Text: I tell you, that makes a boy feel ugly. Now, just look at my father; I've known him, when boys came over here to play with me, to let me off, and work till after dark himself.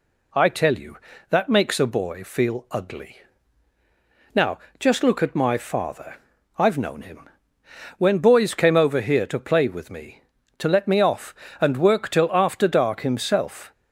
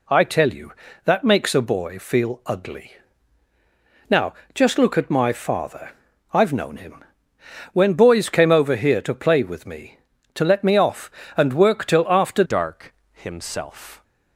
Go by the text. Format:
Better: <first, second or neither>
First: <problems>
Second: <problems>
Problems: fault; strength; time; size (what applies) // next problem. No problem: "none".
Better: first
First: none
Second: changes voice at "dark"; from 12.4 s on; 1.6 s long // pauses between "dark" and "himself"; slight; at 12.9 s; 0.18 s long